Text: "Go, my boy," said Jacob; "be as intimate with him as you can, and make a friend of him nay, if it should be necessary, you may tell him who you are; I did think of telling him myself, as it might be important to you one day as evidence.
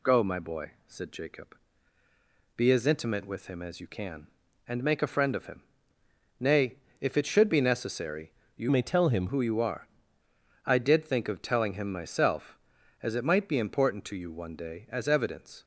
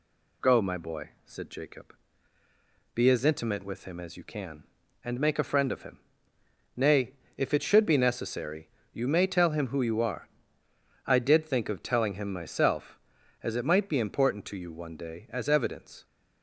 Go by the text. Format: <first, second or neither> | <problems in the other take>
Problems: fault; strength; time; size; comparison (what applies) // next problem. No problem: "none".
second | pauses between "him" and "nay"; noticeable; at 5.6 s; 0.78 s long; noticeable in the second // changes voice from "may" to "him"; from 8.7 to 9.2 s; 0.5 s long